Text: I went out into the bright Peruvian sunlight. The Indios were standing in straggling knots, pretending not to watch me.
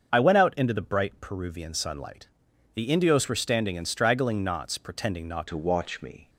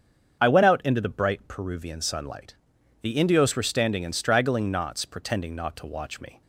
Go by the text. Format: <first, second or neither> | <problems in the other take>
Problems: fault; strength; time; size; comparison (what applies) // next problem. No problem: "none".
second | starts louder than the rest; until 1.1 s; 7 dB; also in the second // changes voice at "to"; from 5.4 s on; 0.8 s long